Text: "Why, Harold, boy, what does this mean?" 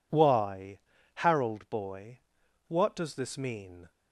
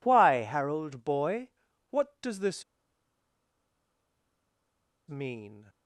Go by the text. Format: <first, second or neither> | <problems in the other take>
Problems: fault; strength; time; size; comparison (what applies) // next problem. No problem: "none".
first | pauses between "this" and "mean"; strong; at 2.6 s; 2.4 s long